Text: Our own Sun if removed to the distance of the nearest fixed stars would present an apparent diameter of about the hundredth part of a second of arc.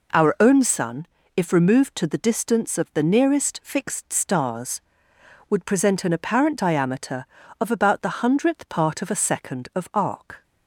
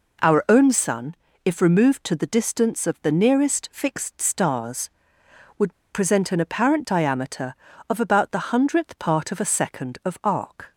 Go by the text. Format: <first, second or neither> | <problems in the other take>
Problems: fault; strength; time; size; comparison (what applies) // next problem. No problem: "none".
first | pauses between "Sun" and "if"; slight; at 1.1 s; 0.30 s long; slight in the first // pauses between "would" and "present"; slight; at 5.7 s; 0.18 s long